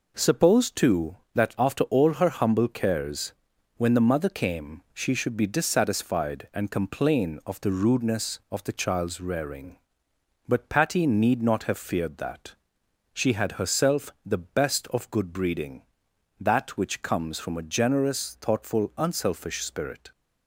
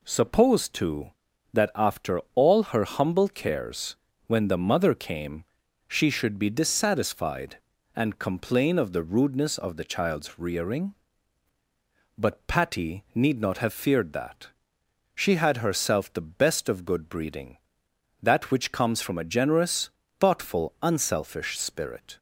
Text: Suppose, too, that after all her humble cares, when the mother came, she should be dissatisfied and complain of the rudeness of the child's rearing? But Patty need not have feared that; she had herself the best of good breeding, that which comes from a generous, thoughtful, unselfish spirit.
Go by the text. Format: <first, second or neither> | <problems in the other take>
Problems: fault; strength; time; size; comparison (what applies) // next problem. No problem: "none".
neither | none